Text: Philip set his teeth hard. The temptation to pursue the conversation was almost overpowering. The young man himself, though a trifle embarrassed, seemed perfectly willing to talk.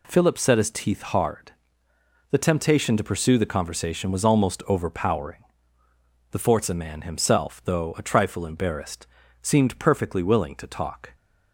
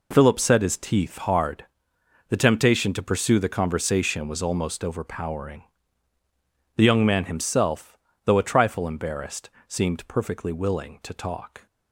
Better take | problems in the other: second | says "forza" for "young"; at 6.3 s

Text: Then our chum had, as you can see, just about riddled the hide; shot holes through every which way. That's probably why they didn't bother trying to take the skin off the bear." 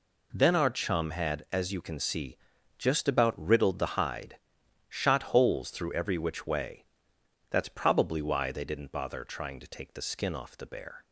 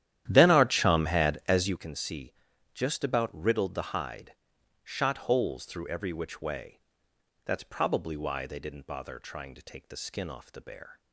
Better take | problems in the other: first | starts louder than the rest; strong; until 1.8 s; 11.5 dB

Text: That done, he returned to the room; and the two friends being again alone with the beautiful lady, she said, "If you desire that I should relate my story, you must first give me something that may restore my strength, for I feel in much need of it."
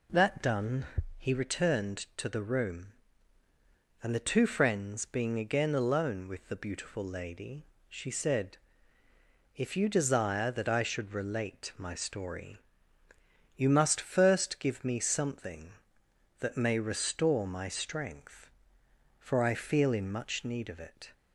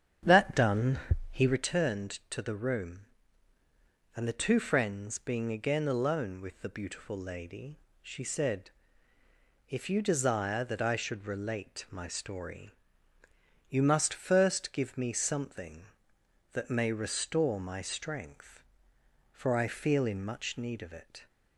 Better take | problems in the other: first | starts louder than the rest; strong; until 1.7 s; 9 dB

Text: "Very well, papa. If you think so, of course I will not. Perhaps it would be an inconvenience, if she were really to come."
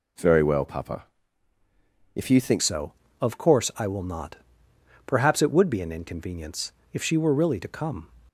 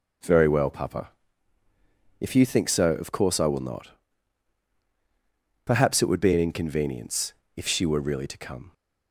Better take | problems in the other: second | changes voice at "so"; from 2.6 s on; 5.4 s long

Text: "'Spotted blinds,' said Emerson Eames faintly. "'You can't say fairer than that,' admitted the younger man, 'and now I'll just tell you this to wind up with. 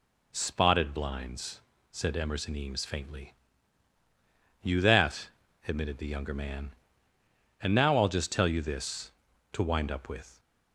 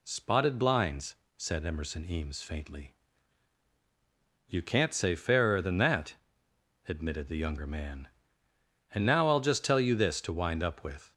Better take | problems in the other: second | skips "can't say fairer than"; at 4.8 s

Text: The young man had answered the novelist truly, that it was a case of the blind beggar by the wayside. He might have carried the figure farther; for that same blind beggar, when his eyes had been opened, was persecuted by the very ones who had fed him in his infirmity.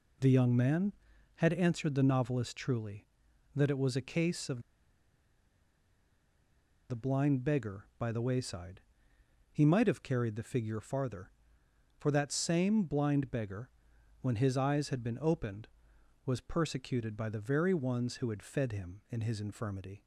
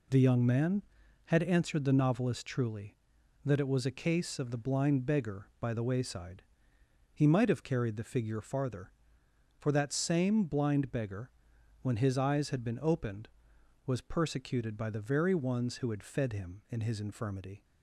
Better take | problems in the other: second | pauses between "of" and "the"; strong; at 4.6 s; 2.2 s long

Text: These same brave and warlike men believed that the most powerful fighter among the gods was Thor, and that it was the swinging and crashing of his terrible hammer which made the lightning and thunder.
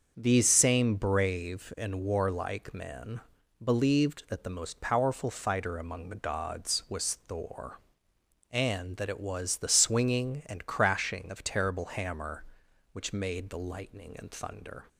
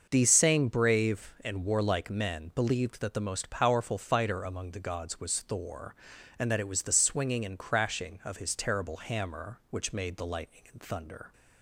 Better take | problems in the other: second | starts louder than the rest; until 1.1 s; 6.5 dB; also in the second // pauses between "men" and "believed"; at 3.1 s; 0.42 s long // skips "his"; at 11.4 s

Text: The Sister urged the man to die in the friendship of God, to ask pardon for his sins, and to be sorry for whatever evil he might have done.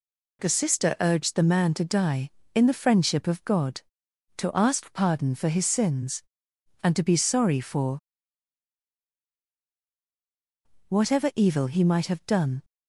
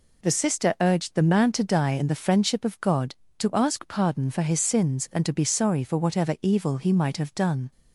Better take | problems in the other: second | pauses between "for" and "whatever"; strong; at 7.9 s; 2.8 s long

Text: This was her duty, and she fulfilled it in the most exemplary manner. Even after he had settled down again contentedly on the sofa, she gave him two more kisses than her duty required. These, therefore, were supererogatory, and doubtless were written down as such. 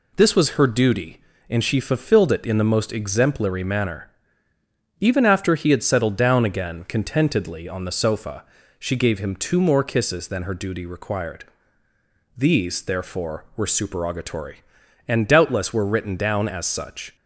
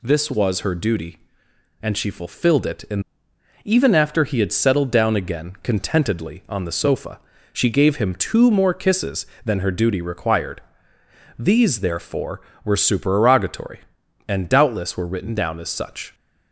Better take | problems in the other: first | skips "the most exemplary manner"; at 3.3 s

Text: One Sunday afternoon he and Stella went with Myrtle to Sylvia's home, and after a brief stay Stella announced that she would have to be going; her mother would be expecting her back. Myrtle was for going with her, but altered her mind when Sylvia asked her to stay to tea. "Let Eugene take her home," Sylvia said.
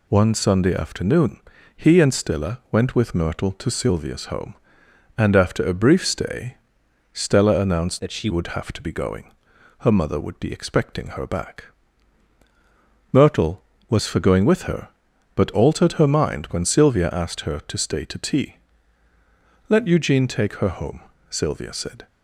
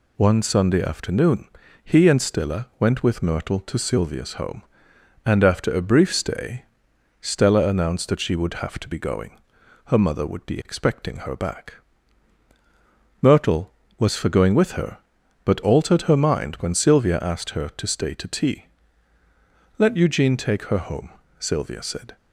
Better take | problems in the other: second | pauses between "afternoon" and "he"; slight; at 1.3 s; 0.36 s long; slight in the second // pauses between "stay" and "Stella"; noticeable; at 6.5 s; 0.54 s long; noticeable in the second // changes voice from "that" to "she"; from 7.9 to 8.2 s; 0.3 s long

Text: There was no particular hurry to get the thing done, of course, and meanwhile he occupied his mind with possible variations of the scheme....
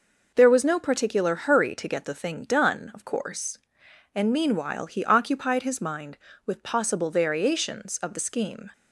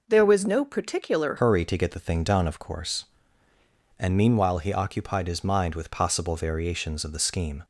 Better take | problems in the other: first | changes voice at "hurry"; from 1.3 s on; 6.3 s long

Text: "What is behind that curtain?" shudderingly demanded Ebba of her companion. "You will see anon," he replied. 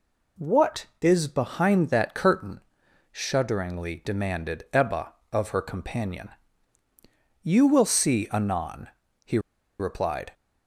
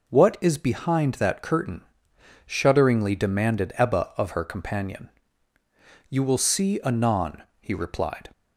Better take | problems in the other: second | pauses between "he" and "replied"; at 9.3 s; 0.40 s long

